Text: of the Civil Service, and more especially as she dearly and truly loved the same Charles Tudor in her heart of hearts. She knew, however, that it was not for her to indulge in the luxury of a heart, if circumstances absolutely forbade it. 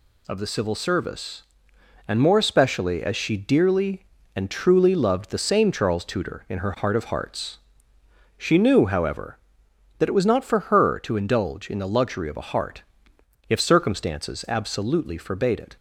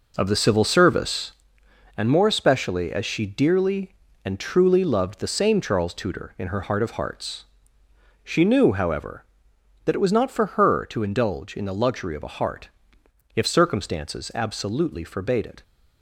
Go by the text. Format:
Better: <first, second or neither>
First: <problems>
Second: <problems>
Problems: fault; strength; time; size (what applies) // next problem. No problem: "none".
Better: first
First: none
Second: starts louder than the rest; noticeable; until 1.5 s; 5 dB